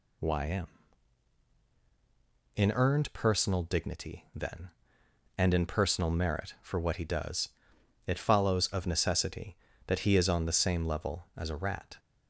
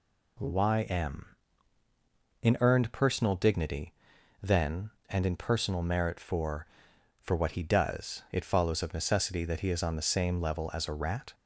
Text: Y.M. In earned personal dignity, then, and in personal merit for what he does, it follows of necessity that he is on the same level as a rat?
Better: first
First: none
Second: says "for" twice; at 7.1 s

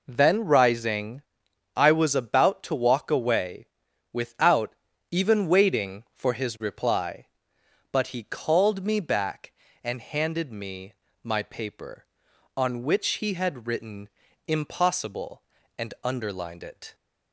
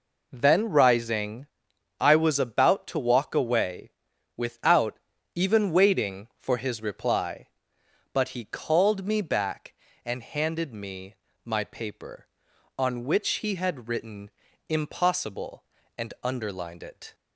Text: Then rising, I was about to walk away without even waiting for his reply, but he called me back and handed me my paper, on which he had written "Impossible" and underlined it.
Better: neither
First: pauses between "away" and "without"; noticeable; at 3.6 s; 0.46 s long // pauses between "without" and "even"; slight; at 4.7 s; 0.36 s long // pauses between "me" and "my"; slight; at 10.9 s; 0.30 s long // pauses between "written" and "Impossible"; at 14.0 s; 0.38 s long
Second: pauses between "away" and "without"; noticeable; at 3.9 s; 0.46 s long // pauses between "without" and "even"; slight; at 4.9 s; 0.36 s long // pauses between "me" and "my"; slight; at 11.1 s; 0.30 s long // pauses between "written" and "Impossible"; at 14.3 s; 0.38 s long

